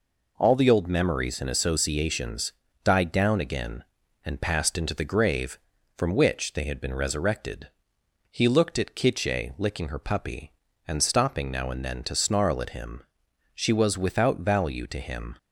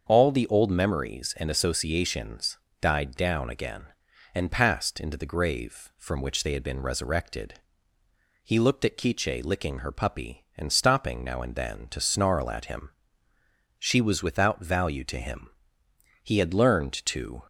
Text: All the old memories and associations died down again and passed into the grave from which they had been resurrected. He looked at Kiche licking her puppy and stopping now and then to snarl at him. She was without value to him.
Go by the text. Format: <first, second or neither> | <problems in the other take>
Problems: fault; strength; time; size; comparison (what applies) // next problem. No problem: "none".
first | starts louder than the rest; until 1.0 s; 6.5 dB // pauses between "associations" and "died"; slight; at 2.5 s; 0.22 s long; slight in the first // goes on to say "He had learned to"; noticeable; from 16.2 s on; 1.2 s long